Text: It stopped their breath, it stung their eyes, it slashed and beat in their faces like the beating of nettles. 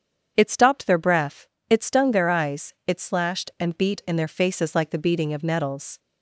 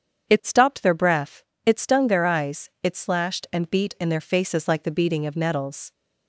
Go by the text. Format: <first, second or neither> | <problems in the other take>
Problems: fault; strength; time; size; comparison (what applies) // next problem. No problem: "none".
neither | starts louder than the rest; strong; the same in both